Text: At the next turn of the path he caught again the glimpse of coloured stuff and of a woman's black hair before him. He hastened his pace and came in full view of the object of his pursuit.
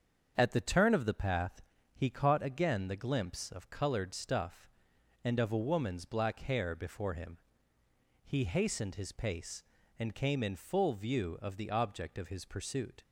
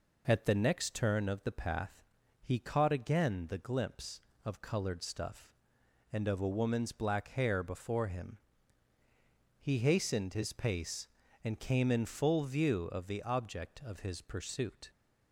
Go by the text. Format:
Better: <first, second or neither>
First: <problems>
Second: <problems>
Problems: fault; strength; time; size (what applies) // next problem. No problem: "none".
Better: second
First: starts louder than the rest; until 1.3 s; 7 dB // skips "next"; at 0.6 s // pauses between "path" and "he"; slight; at 1.6 s; 0.32 s long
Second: pauses between "path" and "he"; at 2.0 s; 0.40 s long